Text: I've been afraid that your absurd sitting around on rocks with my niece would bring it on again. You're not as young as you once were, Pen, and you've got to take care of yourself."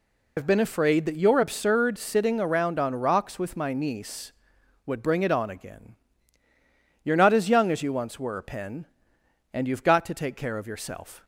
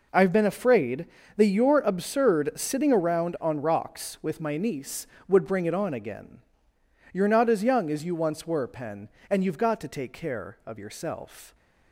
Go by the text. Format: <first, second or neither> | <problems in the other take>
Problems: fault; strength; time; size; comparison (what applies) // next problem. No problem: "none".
second | loses the start of "I've"; at 0.3 s; 100 ms